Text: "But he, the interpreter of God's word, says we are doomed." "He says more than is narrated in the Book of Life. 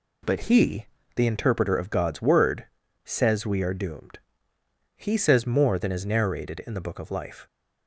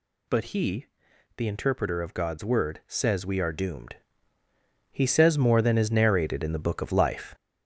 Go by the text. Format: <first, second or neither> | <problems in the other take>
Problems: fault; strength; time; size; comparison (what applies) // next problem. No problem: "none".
first | gets louder; noticeable; throughout; 4.5 dB